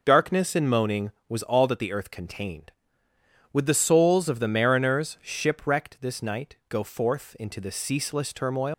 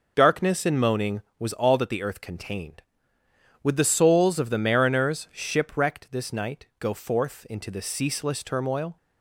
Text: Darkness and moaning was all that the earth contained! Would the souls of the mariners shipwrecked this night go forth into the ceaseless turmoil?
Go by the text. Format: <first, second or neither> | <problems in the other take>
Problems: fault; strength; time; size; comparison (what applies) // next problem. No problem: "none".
second | leaves "turmoil" unfinished; at 8.7 s; 120 ms